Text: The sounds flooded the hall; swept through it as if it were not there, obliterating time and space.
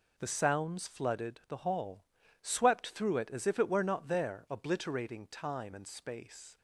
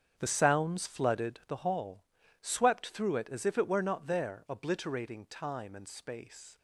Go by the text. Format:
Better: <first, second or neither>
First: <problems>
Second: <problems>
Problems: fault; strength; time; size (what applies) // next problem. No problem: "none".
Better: first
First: none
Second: starts louder than the rest; strong; until 1.8 s; 8 dB